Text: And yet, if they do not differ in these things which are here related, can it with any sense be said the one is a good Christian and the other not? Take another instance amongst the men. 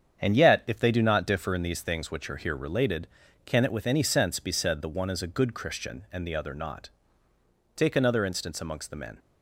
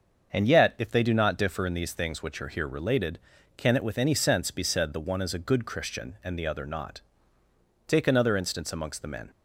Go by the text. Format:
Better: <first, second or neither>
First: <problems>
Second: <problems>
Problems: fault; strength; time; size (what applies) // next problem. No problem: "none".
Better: second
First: gets quieter; throughout; 7 dB // starts louder than the rest; strong; until 1.2 s; 8 dB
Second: starts louder than the rest; until 1.3 s; 6.5 dB